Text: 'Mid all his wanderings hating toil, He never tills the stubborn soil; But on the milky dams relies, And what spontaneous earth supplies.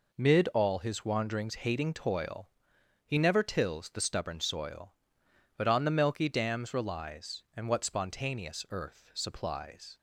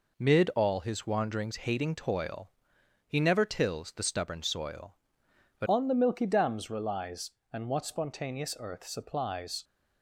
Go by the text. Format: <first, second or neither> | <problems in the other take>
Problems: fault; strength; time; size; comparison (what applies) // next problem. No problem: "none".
first | changes voice at "on"; from 5.6 s on; 4.0 s long